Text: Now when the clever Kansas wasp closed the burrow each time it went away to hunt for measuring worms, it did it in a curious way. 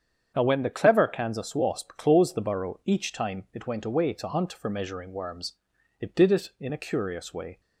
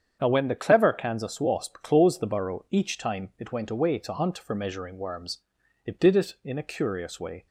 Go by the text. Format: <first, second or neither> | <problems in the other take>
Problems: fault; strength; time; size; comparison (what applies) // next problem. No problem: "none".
neither | starts louder than the rest; strong; the same in both